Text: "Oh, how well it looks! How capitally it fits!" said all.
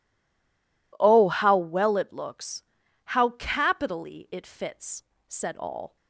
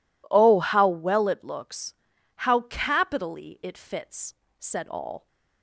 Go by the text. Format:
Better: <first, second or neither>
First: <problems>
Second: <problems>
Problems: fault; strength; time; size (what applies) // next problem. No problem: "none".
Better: second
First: stays silent before the first word; slight; until 0.9 s; 0.9 s long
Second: none